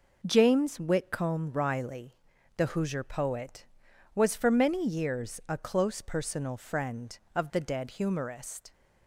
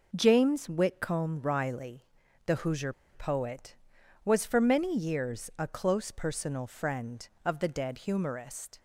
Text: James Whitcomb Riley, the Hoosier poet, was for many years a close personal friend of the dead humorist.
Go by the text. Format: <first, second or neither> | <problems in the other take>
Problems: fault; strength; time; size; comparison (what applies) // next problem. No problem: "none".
first | pauses between "Hoosier" and "poet"; slight; at 2.9 s; 0.21 s long